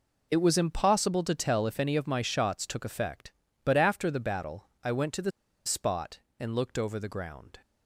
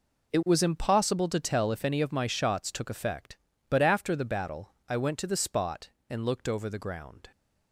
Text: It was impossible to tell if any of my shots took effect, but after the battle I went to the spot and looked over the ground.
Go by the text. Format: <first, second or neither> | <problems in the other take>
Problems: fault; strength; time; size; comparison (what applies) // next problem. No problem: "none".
second | pauses between "battle" and "I"; slight; at 4.6 s; 0.16 s long; slight in the second // pauses between "the" and "spot"; slight; at 5.3 s; 0.35 s long